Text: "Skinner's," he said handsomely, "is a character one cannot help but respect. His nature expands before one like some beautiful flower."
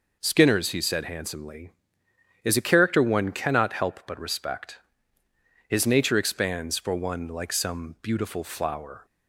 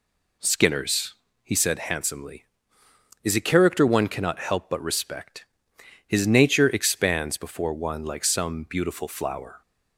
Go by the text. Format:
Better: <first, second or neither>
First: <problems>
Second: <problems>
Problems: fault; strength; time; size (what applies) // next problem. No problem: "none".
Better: second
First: says "for" for "before"; at 6.7 s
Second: none